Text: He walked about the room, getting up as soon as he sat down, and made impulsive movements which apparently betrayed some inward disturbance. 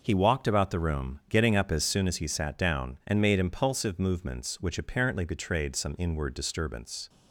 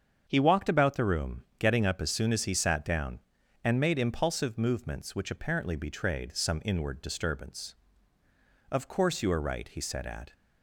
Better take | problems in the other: first | starts louder than the rest; until 1.2 s; 7 dB // goes on to say "Of course you are right he said at"; from 8.6 s on; 1.6 s long

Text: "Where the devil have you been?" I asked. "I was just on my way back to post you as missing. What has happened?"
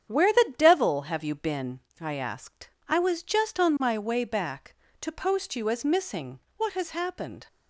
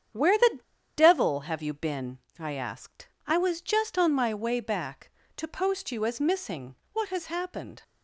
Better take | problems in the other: first | starts louder than the rest; strong; until 1.5 s; 8.5 dB; strong in the first // pauses between "the" and "devil"; at 0.5 s; 0.37 s long

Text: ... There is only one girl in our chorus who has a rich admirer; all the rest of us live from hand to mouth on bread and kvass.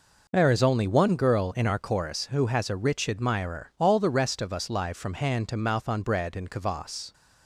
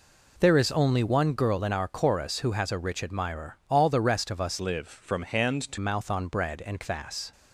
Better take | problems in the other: first | changes voice from "live" to "to"; from 4.5 to 5.7 s; 1.2 s long

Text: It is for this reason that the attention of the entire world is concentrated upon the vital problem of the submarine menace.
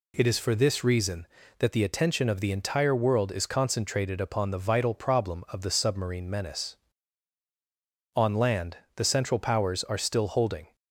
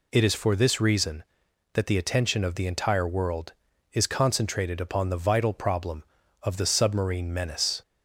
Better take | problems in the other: second | goes on to say "On land the Central Powers are still holding"; strong; from 8.1 s on; 2.6 s long

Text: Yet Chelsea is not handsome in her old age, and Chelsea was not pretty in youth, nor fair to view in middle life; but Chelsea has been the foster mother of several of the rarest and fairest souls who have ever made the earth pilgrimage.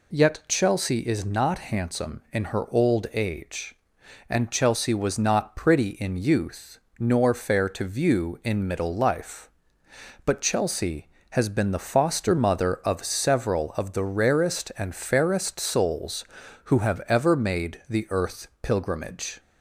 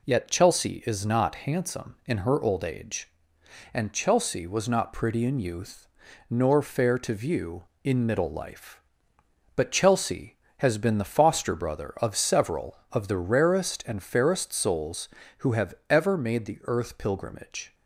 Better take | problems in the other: first | says "brother" for "mother"; at 11.5 s // pauses between "have" and "ever"; slight; at 15.7 s; 0.16 s long

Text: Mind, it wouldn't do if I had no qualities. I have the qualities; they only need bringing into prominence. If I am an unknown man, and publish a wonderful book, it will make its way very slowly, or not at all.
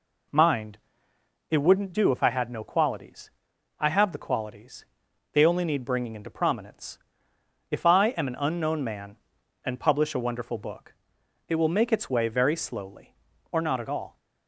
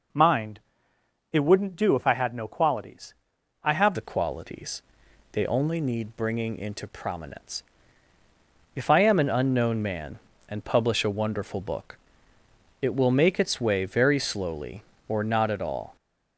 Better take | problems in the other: first | changes voice at "the"; from 3.9 s on; 12.0 s long

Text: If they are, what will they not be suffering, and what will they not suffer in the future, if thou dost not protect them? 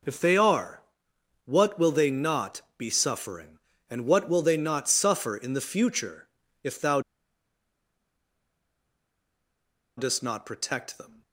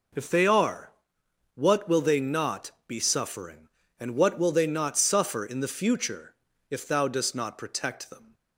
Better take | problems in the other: second | pauses between "not" and "be"; slight; at 2.5 s; 0.16 s long; slight in the second // pauses between "thou" and "dost"; strong; at 6.9 s; 2.9 s long

